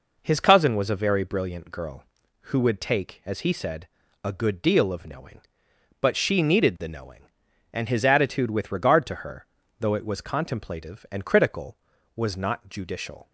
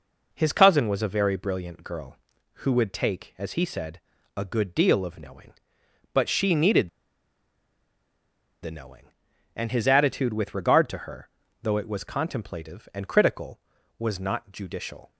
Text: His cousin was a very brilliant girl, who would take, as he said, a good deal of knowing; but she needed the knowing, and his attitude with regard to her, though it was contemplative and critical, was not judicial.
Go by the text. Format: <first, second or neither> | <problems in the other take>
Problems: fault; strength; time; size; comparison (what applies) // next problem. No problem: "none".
first | pauses between "needed" and "the"; strong; at 6.8 s; 1.7 s long